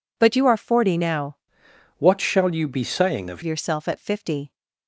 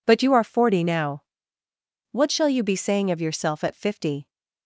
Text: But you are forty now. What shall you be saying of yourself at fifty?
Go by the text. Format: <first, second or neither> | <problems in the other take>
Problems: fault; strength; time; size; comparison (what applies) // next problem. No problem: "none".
second | changes voice from "What" to "of"; from 1.9 to 3.4 s; 1.5 s long